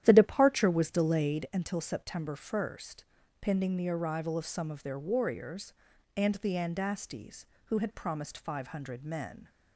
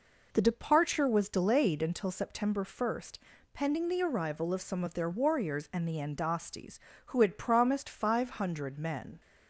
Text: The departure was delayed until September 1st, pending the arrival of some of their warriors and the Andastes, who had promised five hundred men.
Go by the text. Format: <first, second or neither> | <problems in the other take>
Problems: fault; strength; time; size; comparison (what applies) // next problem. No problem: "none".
second | starts louder than the rest; strong; until 1.5 s; 11 dB